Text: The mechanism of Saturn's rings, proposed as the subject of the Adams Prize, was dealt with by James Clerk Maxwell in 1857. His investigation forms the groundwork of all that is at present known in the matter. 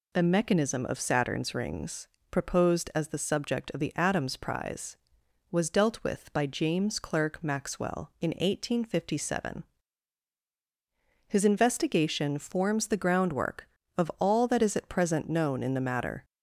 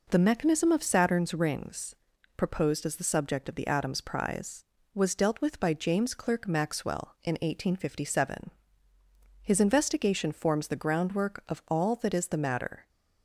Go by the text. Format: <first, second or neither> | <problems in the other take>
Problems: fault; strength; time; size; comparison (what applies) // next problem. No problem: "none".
first | skips "at present known in"; at 12.2 s